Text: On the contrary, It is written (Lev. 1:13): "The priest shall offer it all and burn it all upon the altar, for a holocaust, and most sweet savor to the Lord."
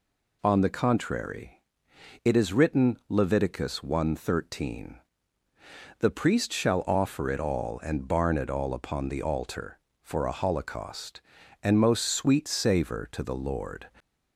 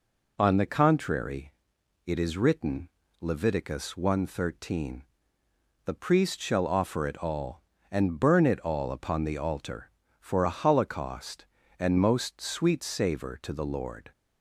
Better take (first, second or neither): second